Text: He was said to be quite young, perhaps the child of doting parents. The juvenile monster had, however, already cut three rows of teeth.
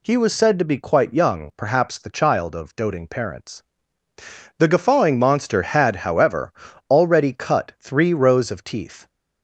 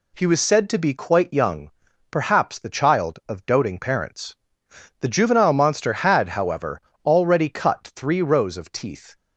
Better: second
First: says "guffawing" for "juvenile"; at 4.6 s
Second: none

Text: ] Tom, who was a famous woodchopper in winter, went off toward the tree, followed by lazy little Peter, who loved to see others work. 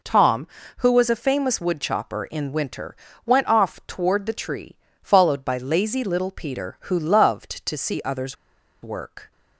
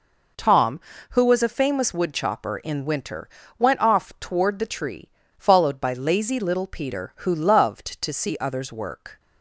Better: second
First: pauses between "others" and "work"; noticeable; at 8.3 s; 0.47 s long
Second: none

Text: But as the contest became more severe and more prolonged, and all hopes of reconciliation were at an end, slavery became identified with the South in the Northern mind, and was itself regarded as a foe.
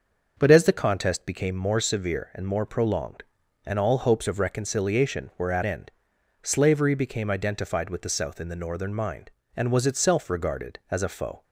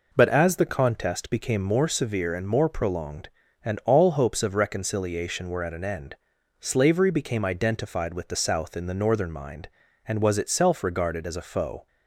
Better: second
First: starts louder than the rest; until 1.3 s; 6 dB // skips "an"; at 5.6 s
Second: none

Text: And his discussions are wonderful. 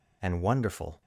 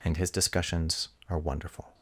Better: second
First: skips "his discussions are"; at 0.4 s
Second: none

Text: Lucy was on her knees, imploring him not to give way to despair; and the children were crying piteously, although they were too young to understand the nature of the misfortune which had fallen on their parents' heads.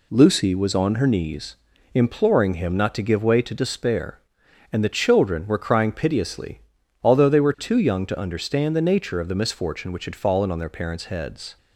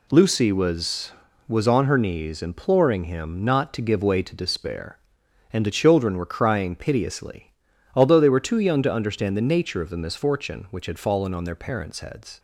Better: first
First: none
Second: says "was" twice; at 1.4 s

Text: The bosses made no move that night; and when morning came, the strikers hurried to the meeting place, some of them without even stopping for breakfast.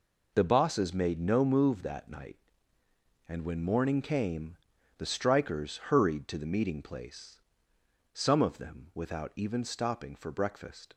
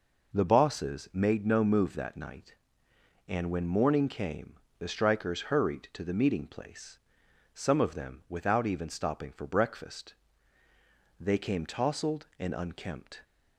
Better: first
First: none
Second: goes on to say "They came tousled and unkempt"; strong; from 11.1 s on; 2.0 s long

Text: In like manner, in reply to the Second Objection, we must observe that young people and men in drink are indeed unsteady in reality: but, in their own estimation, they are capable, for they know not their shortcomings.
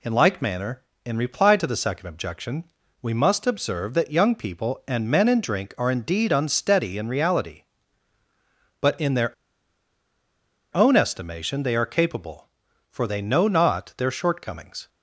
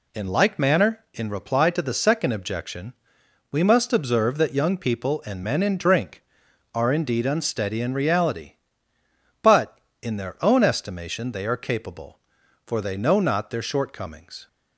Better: second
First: pauses between "their" and "own"; strong; at 9.3 s; 1.4 s long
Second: none

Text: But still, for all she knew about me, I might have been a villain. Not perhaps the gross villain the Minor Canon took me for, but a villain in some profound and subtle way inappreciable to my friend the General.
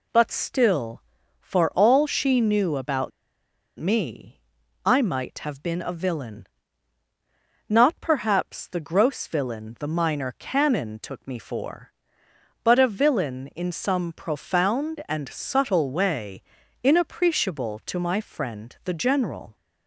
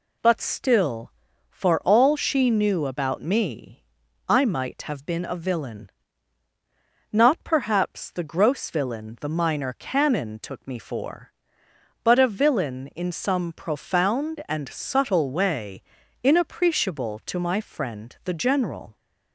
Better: second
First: pauses between "about" and "me"; noticeable; at 3.1 s; 0.68 s long // pauses between "way" and "inappreciable"; at 16.4 s; 0.40 s long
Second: pauses between "way" and "inappreciable"; at 15.8 s; 0.40 s long

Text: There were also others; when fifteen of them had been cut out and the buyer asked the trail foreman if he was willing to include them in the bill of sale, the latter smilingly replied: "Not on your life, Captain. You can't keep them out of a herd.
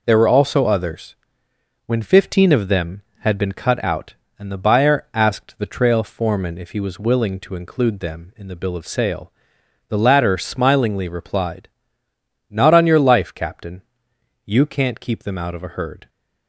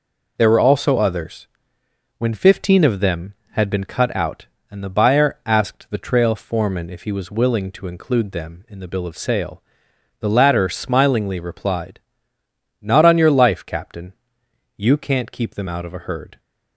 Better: neither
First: none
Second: none

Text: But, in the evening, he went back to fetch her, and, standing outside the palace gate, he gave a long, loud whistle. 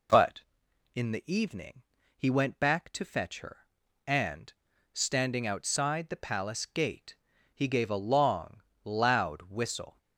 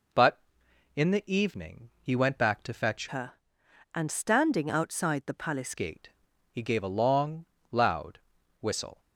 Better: first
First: none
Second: changes voice from "her" to "palace"; from 3.0 to 5.7 s; 2.7 s long // pauses between "loud" and "whistle"; at 8.1 s; 0.42 s long

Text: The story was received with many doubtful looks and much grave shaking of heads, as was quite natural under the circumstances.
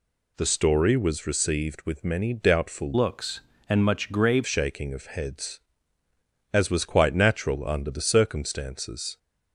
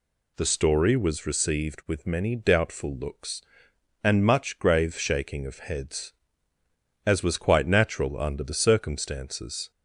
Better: second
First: changes voice from "looks" to "grave"; from 2.9 to 4.4 s; 1.5 s long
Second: none

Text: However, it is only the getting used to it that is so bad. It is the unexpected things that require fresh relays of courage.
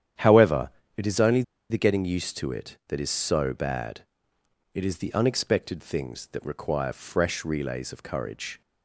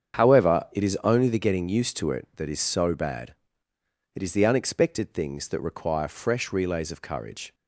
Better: second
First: starts louder than the rest; strong; until 1.7 s; 10 dB // pauses between "only" and "the"; slight; at 1.4 s; 0.28 s long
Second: starts louder than the rest; strong; until 1.2 s; 7.5 dB

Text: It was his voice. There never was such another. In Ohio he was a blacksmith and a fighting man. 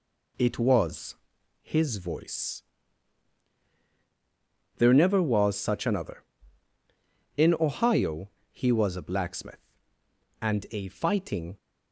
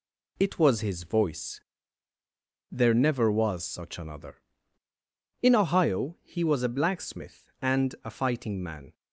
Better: second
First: pauses between "was" and "his"; noticeable; at 1.1 s; 0.48 s long // pauses between "Ohio" and "he"; slight; at 8.2 s; 0.22 s long // stops before "man"; at 11.5 s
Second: none

